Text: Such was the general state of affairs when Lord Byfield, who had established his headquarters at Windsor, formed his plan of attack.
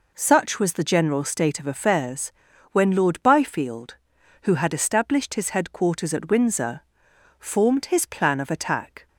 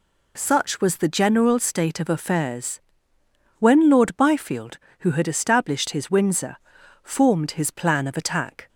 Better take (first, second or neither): first